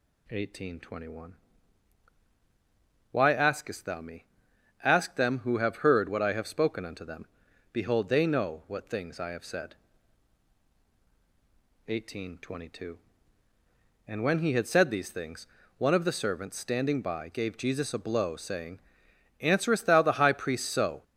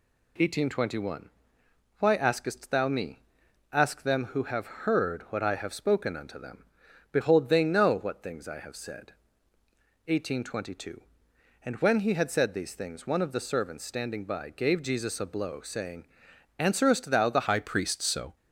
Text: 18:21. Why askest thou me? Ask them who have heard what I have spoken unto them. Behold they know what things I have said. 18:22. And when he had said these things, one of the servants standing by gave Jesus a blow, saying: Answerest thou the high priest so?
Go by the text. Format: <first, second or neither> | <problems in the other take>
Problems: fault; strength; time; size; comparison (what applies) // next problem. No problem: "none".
first | changes voice at "high"; from 17.4 s on; 0.9 s long